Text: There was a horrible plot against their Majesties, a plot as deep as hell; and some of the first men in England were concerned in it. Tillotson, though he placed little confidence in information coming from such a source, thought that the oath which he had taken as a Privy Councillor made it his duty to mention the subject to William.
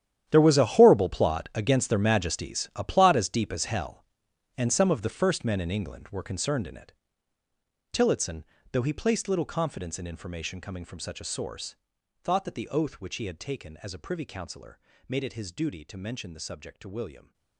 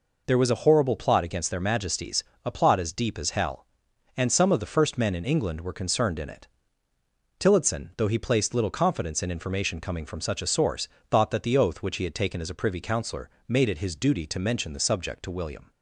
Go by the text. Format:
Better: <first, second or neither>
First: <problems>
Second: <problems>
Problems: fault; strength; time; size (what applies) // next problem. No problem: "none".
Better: second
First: gets quieter; strong; throughout; 16 dB // pauses between "Councillor" and "made"; slight; at 14.7 s; 0.28 s long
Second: pauses between "Councillor" and "made"; slight; at 13.3 s; 0.16 s long